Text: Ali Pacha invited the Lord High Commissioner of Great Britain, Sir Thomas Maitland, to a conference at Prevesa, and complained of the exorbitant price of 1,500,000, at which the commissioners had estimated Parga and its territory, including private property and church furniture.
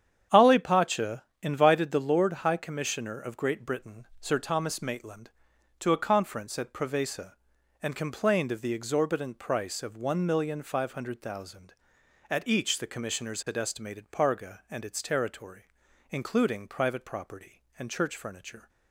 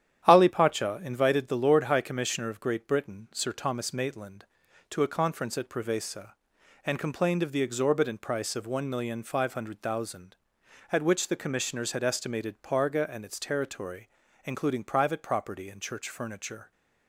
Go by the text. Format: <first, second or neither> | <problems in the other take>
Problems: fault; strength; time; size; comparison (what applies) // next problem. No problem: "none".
second | starts louder than the rest; strong; until 1.5 s; 9 dB; strong in the second // pauses between "Pacha" and "invited"; slight; at 1.2 s; 0.20 s long // says "each" for "which"; at 12.4 s